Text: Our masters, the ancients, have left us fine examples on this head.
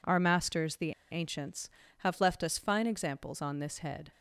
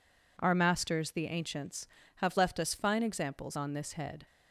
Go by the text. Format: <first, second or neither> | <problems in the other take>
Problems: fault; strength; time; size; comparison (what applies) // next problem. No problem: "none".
second | pauses between "the" and "ancients"; slight; at 0.9 s; 0.19 s long